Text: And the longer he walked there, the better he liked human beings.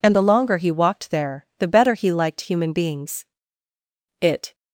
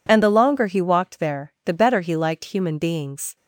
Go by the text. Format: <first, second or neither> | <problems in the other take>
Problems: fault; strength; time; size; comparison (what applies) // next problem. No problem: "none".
second | goes on to say "It"; slight; from 4.2 s on; 0.34 s long